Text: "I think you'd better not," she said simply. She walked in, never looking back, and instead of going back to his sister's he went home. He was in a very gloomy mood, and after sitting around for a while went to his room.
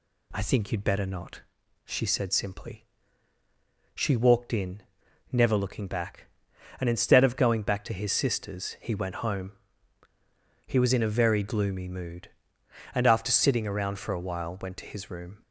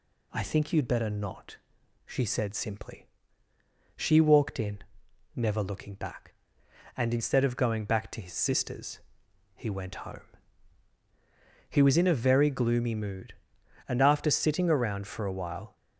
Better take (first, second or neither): first